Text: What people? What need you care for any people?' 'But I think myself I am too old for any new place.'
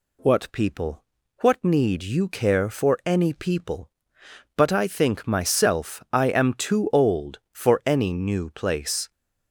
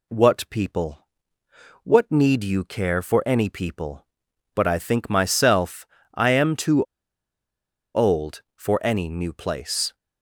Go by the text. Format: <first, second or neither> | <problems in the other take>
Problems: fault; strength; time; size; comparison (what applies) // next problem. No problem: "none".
first | pauses between "myself" and "I"; slight; at 5.8 s; 0.30 s long // pauses between "too" and "old"; at 6.8 s; 1.1 s long